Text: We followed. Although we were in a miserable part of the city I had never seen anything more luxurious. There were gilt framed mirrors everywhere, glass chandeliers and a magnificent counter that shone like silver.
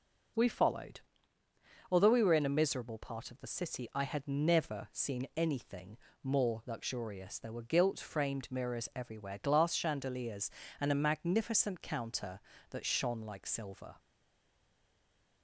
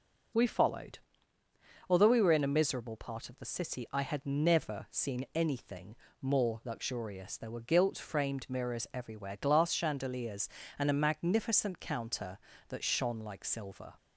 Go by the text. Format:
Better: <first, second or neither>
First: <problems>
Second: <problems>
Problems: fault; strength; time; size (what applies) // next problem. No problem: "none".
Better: second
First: pauses between "anything" and "more"; slight; at 5.9 s; 0.28 s long // stays silent after the last word; noticeable; from 13.9 s on; 1.5 s long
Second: pauses between "anything" and "more"; slight; at 5.9 s; 0.28 s long